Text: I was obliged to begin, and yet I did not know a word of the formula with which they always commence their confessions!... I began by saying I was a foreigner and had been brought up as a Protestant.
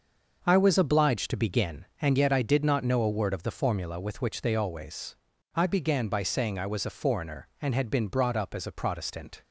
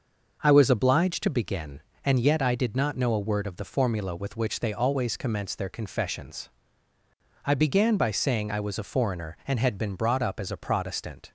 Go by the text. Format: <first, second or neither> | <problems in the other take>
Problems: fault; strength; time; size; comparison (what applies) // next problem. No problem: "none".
second | starts louder than the rest; until 1.4 s; 6 dB; noticeable in the second // skips "commence their confessions"; at 5.3 s